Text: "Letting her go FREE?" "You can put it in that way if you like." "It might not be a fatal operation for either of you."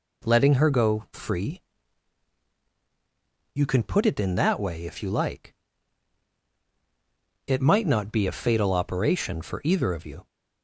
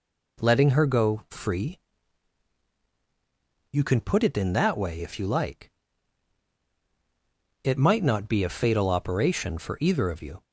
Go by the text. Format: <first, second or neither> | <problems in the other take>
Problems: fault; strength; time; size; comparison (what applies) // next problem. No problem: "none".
neither | none